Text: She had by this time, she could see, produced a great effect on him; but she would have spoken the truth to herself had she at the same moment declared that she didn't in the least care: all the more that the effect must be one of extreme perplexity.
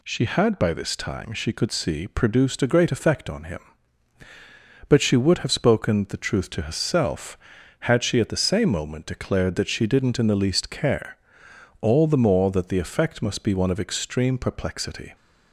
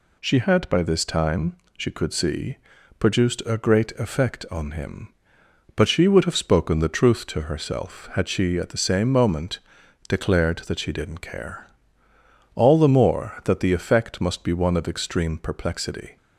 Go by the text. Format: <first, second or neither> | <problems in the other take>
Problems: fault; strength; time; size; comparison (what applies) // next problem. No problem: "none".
first | pauses between "moment" and "declared"; noticeable; at 9.6 s; 0.48 s long // skips "in the least"; at 11.2 s